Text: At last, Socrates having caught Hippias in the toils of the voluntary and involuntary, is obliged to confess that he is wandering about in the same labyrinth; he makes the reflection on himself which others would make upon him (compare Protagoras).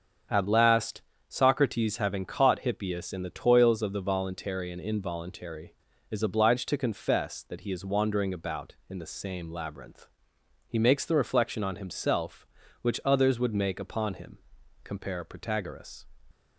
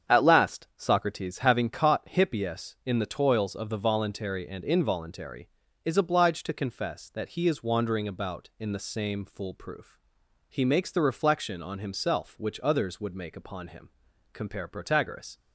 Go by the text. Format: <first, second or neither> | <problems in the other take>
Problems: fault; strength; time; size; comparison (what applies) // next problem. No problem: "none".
first | starts louder than the rest; strong; until 1.2 s; 8 dB; also in the first // says "foolproof" for "labyrinth"; at 9.2 s